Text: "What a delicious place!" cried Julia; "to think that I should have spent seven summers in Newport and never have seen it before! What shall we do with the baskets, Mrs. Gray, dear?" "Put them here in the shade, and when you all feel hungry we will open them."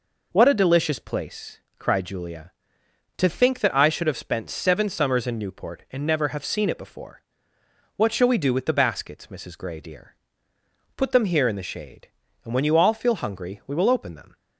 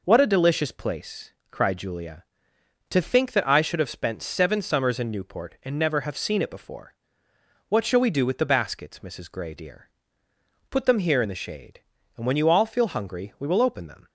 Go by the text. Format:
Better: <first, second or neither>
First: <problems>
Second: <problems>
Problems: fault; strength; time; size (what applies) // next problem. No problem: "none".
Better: neither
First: none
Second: none